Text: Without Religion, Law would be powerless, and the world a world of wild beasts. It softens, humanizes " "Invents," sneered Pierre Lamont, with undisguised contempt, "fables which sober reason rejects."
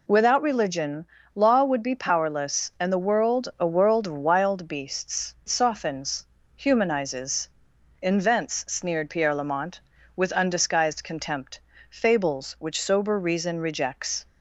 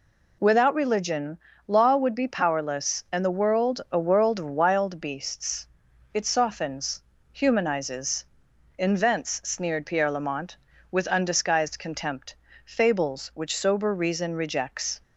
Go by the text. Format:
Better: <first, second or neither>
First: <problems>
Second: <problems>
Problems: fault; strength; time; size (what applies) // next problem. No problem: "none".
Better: second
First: skips "It"; at 5.4 s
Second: none